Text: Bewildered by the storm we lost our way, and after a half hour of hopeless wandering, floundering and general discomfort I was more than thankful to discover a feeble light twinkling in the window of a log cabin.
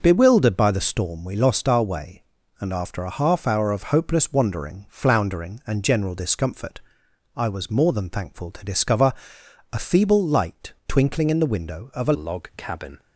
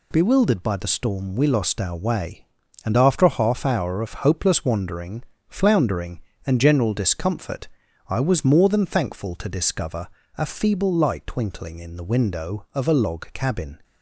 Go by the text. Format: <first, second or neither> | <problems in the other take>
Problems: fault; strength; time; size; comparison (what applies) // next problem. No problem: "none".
second | pauses between "discomfort" and "I"; noticeable; at 6.7 s; 0.56 s long; also in the second // pauses between "discover" and "a"; noticeable; at 9.1 s; 0.58 s long; slight in the second // changes voice at "log"; from 12.1 s on; 0.8 s long